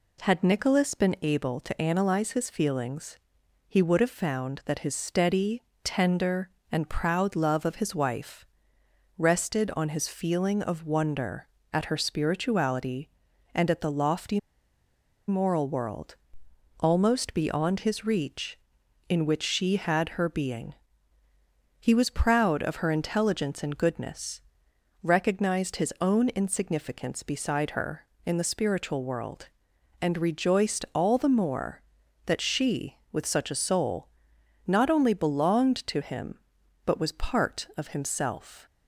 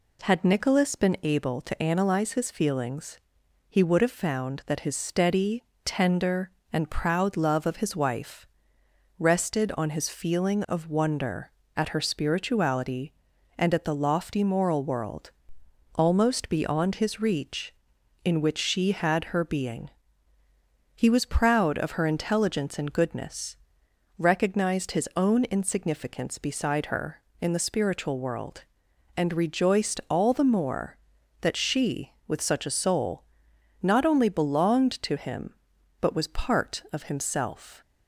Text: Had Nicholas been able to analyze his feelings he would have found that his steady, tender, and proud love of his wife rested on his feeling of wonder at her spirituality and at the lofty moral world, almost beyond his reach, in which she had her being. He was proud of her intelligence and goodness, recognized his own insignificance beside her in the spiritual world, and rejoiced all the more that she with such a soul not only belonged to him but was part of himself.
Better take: second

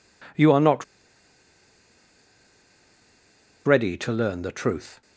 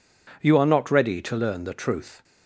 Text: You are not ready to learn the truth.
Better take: second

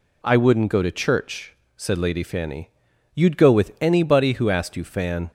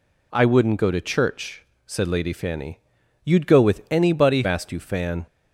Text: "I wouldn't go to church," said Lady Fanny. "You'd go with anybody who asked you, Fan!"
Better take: first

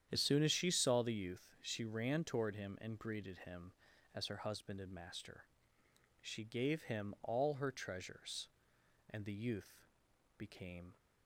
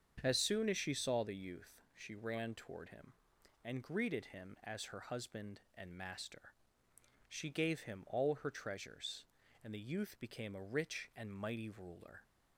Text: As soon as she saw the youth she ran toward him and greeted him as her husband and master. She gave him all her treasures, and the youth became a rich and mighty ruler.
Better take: second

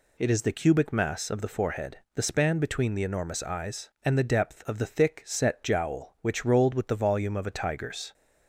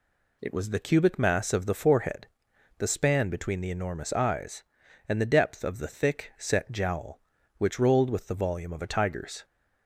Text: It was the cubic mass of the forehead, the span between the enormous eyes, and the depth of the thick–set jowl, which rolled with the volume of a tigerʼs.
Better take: second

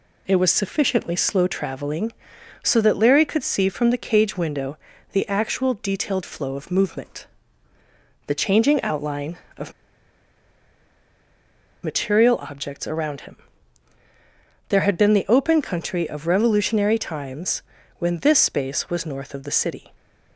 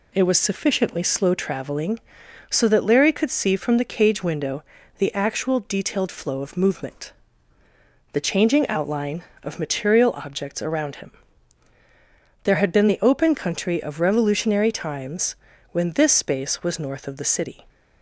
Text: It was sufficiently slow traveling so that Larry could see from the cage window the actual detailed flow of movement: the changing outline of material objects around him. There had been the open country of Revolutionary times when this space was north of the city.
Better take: second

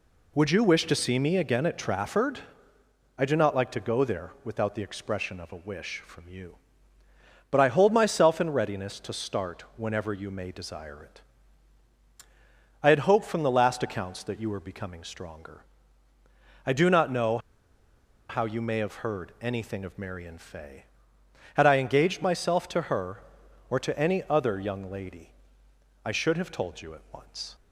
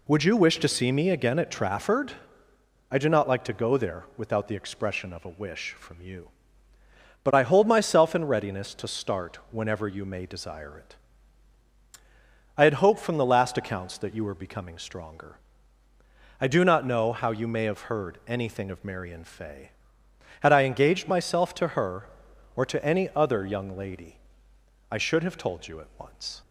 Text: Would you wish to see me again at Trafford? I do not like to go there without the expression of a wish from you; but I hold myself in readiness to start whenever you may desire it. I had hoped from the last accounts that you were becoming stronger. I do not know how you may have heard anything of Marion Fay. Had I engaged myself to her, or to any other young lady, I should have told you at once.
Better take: second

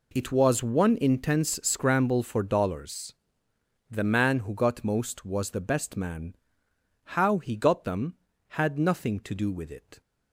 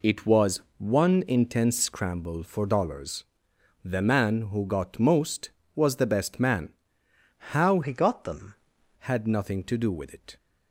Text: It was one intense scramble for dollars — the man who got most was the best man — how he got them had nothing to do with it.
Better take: first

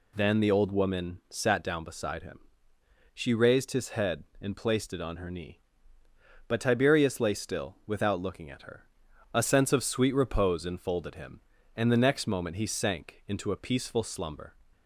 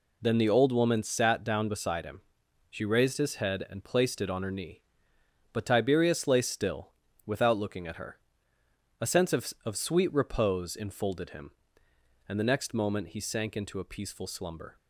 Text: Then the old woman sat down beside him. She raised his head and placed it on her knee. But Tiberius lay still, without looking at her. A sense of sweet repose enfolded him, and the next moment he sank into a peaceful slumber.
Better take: first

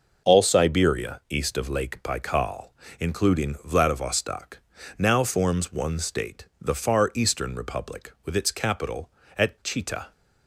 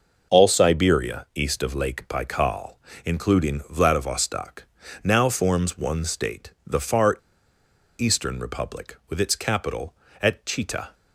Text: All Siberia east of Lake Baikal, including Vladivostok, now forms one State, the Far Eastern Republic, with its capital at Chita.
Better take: first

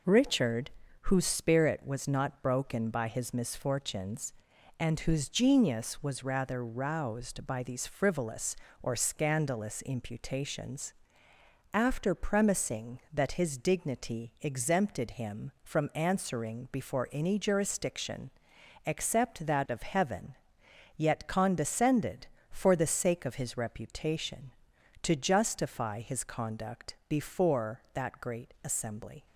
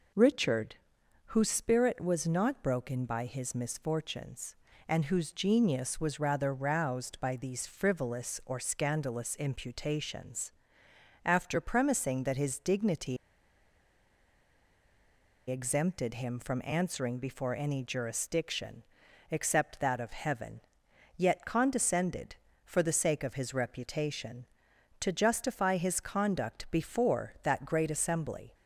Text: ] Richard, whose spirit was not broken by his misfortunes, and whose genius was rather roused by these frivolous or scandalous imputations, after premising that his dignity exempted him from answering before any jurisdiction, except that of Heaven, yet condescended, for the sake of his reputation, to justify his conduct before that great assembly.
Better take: first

